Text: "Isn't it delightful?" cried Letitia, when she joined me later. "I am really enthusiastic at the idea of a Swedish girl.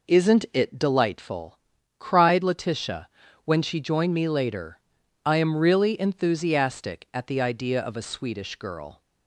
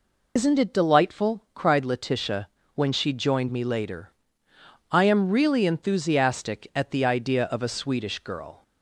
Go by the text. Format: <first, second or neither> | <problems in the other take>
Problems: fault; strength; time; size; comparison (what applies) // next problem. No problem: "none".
first | loses the start of "Isn't"; at 0.3 s; 100 ms